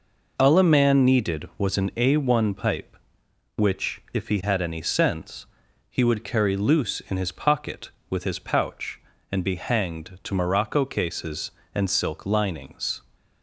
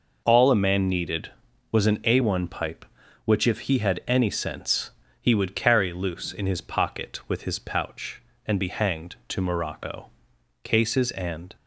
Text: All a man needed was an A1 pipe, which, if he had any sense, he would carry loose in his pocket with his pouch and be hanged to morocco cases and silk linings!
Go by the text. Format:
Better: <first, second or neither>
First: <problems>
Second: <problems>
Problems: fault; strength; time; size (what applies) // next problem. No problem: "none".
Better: first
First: none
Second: pauses between "morocco" and "cases"; noticeable; at 10.0 s; 0.54 s long // stops before "silk linings"; at 11.5 s